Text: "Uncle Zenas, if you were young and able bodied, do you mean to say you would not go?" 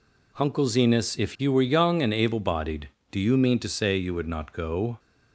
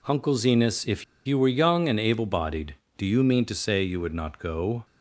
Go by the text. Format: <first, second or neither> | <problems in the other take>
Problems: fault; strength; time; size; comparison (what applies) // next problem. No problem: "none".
first | pauses between "if" and "you"; slight; at 1.0 s; 0.22 s long